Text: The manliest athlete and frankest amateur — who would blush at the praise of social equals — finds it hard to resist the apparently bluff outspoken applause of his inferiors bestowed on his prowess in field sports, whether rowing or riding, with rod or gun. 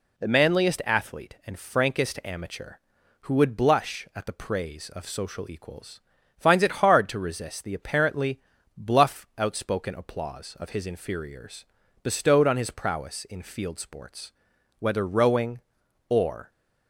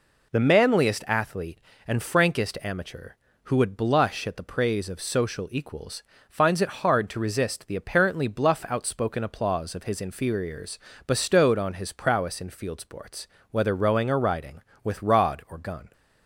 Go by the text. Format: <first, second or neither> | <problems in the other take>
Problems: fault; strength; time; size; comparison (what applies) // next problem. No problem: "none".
second | pauses between "apparently" and "bluff"; at 8.4 s; 0.38 s long // pauses between "inferiors" and "bestowed"; slight; at 11.6 s; 0.36 s long; slight in the second // stops before "riding with rod or gun"; at 16.5 s